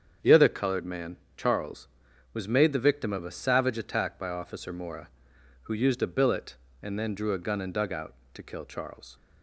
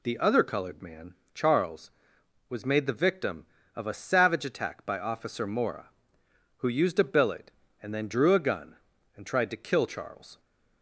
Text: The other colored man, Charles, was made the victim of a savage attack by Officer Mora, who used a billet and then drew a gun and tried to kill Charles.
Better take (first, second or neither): second